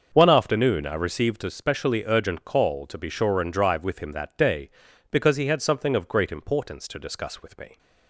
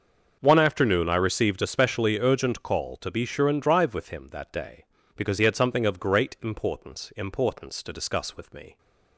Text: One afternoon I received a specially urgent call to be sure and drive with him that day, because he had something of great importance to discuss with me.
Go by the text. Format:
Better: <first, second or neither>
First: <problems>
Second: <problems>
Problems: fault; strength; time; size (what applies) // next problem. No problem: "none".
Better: first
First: starts louder than the rest; until 1.1 s; 6.5 dB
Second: starts louder than the rest; until 1.4 s; 6.5 dB // says "importance" twice; at 7.1 s